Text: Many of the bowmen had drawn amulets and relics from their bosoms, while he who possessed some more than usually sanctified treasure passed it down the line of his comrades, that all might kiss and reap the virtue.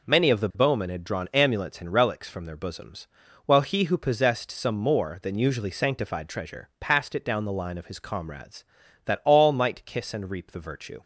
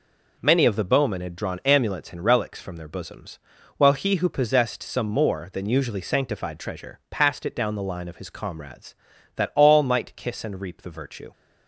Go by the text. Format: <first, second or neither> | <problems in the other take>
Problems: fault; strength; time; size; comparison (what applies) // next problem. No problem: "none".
neither | none